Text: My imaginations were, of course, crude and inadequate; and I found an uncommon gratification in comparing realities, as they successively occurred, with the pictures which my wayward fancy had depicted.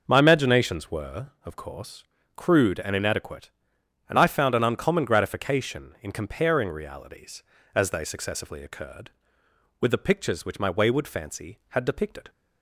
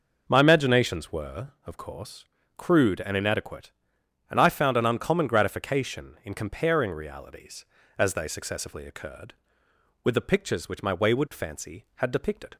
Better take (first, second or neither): neither